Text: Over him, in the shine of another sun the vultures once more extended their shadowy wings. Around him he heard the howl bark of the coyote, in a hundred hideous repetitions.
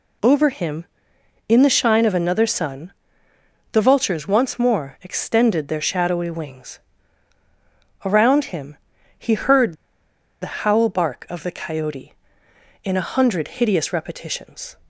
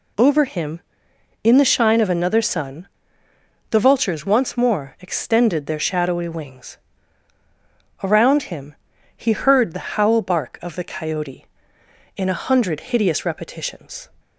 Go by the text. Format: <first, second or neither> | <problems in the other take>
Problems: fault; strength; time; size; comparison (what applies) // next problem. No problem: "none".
second | pauses between "sun" and "the"; noticeable; at 2.9 s; 0.80 s long; noticeable in the second // pauses between "him" and "he"; at 8.7 s; 0.42 s long; also in the second // pauses between "heard" and "the"; noticeable; at 9.7 s; 0.66 s long